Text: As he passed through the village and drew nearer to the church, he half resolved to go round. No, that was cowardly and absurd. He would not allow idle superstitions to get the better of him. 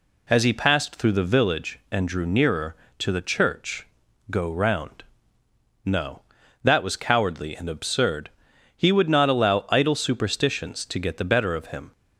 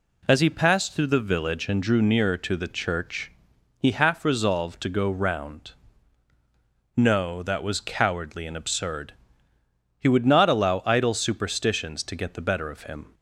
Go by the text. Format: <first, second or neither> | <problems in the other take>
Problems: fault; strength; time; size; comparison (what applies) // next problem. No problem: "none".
second | skips "he half resolved to"; at 4.0 s